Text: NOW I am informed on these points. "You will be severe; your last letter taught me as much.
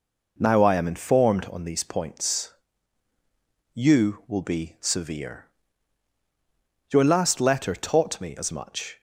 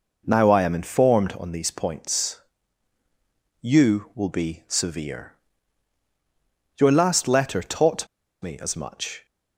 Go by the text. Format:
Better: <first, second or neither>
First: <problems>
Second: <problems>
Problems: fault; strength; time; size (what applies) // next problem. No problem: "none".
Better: first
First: none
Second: pauses between "taught" and "me"; slight; at 8.0 s; 0.36 s long